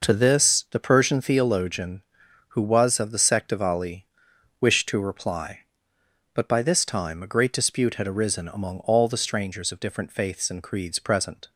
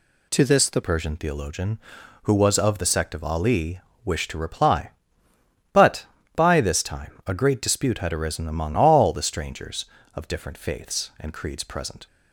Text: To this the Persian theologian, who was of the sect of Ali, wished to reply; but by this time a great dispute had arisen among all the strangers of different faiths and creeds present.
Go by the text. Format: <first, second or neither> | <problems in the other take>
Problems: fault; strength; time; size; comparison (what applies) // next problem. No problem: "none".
first | changes voice at "Persian"; from 0.8 s on; 11.2 s long